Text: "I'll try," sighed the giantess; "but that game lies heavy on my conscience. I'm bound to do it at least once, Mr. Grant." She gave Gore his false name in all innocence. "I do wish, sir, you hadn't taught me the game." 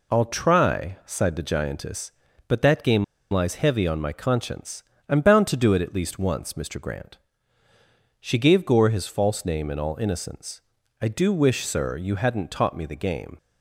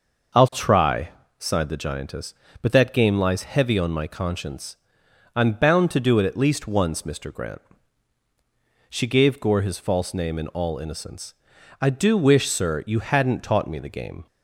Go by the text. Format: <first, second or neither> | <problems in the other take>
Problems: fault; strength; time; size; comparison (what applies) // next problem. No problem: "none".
second | pauses between "game" and "lies"; slight; at 3.0 s; 0.26 s long